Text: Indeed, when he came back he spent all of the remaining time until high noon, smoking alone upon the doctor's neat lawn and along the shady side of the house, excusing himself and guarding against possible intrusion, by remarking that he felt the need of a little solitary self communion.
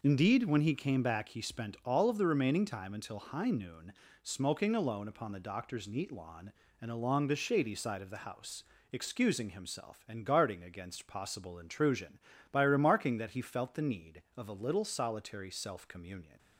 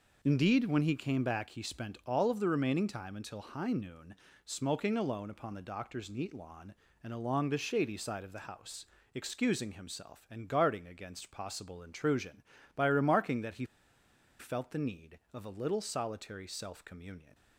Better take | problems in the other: first | pauses between "he" and "felt"; noticeable; at 13.6 s; 0.73 s long

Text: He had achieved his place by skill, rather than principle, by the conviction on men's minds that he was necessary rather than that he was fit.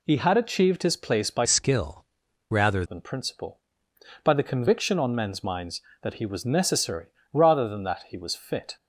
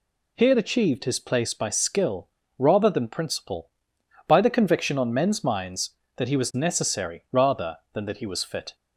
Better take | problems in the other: second | changes voice from "skill" to "rather"; from 1.4 to 2.8 s; 1.4 s long // pauses between "necessary" and "rather"; slight; at 7.0 s; 0.26 s long

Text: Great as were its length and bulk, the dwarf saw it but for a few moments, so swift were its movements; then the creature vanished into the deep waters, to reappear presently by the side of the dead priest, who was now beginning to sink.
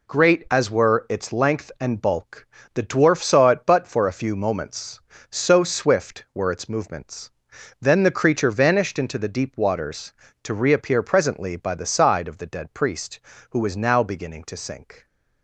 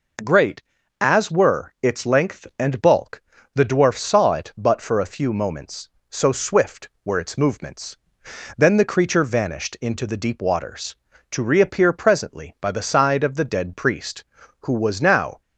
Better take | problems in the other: first | stops before "beginning to sink"; at 15.4 s

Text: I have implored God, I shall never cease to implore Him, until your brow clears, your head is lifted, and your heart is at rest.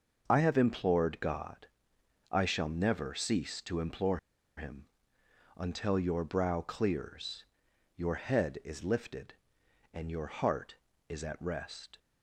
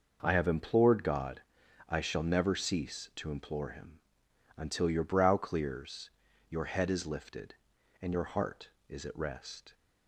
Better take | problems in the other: second | starts louder than the rest; noticeable; until 1.2 s; 6 dB // pauses between "implore" and "Him"; at 4.1 s; 0.38 s long

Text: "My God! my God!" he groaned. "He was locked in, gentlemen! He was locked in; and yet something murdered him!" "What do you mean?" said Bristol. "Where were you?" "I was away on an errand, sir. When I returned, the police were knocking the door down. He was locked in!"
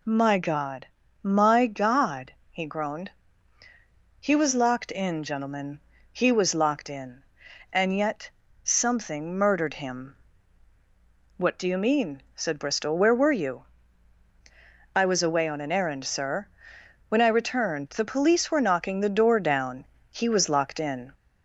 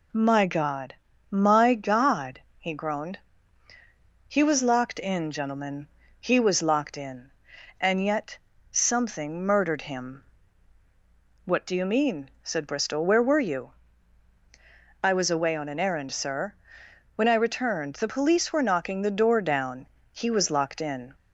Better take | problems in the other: second | gets louder; slight; throughout; 2 dB // pauses between "yet" and "something"; slight; at 8.2 s; 0.36 s long; slight in the second

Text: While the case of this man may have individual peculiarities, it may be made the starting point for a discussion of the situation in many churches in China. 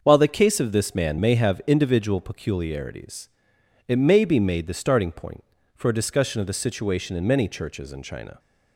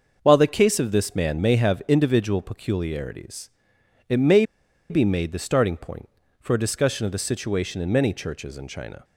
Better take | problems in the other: first | starts louder than the rest; until 1.2 s; 6.5 dB; also in the first // pauses between "may" and "be"; noticeable; at 4.4 s; 0.46 s long

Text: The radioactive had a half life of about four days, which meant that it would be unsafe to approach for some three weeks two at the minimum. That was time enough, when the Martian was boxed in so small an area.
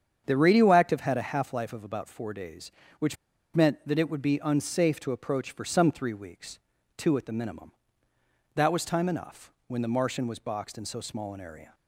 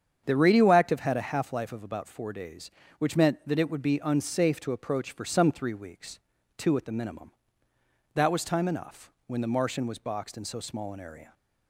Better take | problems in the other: second | starts louder than the rest; strong; until 1.2 s; 8 dB; strong in the second // pauses between "which" and "meant"; at 3.1 s; 0.39 s long // pauses between "weeks" and "two"; at 6.5 s; 0.40 s long; also in the second

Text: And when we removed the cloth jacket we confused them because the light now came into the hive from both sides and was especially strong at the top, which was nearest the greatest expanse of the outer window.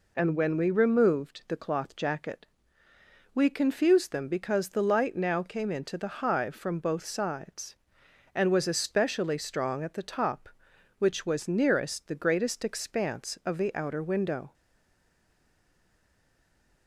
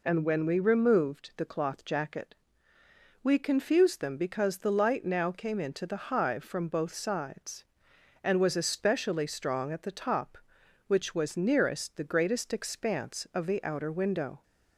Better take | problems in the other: second | pauses between "jacket" and "we"; noticeable; at 2.4 s; 0.88 s long; noticeable in the second // stays silent after the last word; from 14.5 s on; 2.3 s long

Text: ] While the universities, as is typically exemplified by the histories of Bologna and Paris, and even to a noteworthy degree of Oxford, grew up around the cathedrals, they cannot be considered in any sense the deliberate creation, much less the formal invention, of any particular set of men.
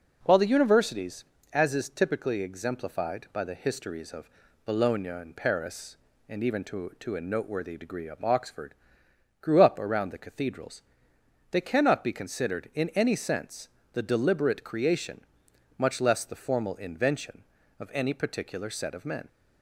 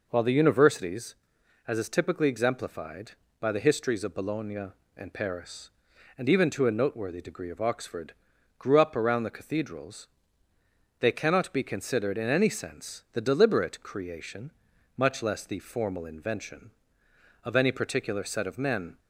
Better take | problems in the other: second | pauses between "of" and "Bologna"; slight; at 4.2 s; 0.36 s long // says "to" twice; at 6.9 s // pauses between "sense" and "the"; slight; at 13.6 s; 0.26 s long

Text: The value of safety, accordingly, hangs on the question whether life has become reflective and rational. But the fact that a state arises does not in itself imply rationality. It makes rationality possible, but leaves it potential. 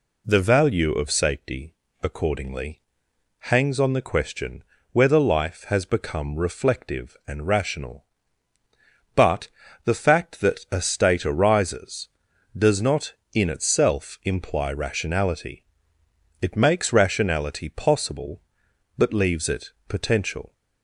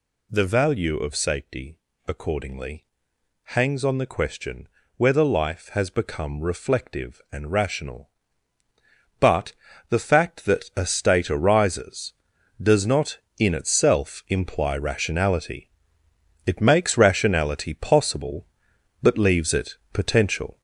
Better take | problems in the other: first | gets louder; noticeable; throughout; 5.5 dB // pauses between "question" and "whether"; slight; at 4.6 s; 0.28 s long; slight in the first // pauses between "But" and "the"; slight; at 9.5 s; 0.34 s long; slight in the first

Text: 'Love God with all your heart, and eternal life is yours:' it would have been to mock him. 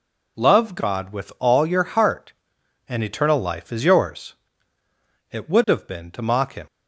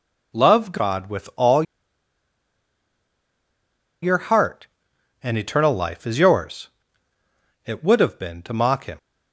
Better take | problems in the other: first | pauses between "all" and "your"; strong; at 1.6 s; 2.4 s long

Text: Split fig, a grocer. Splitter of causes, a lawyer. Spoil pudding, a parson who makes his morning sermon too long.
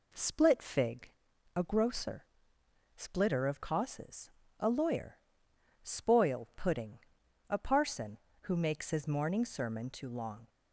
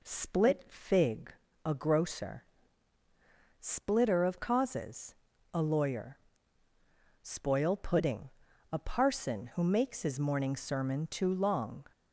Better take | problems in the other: neither | none

